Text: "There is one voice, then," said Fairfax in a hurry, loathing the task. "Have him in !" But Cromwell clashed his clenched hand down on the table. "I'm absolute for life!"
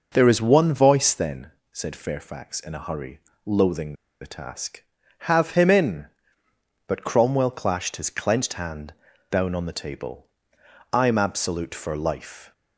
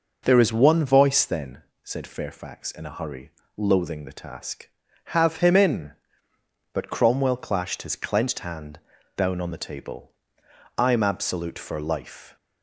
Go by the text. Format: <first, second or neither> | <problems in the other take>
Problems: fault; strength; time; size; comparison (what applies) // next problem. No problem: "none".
second | starts louder than the rest; noticeable; until 1.1 s; 6 dB // pauses between "loathing" and "the"; slight; at 3.9 s; 0.26 s long // pauses between "hand" and "down"; at 8.9 s; 0.38 s long; also in the second